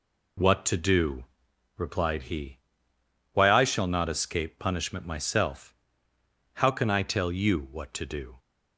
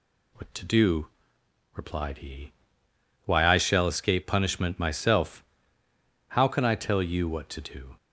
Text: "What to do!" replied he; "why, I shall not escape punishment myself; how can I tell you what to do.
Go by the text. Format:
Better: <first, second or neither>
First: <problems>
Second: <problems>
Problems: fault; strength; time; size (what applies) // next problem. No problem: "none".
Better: first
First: none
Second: skips "not"; at 3.8 s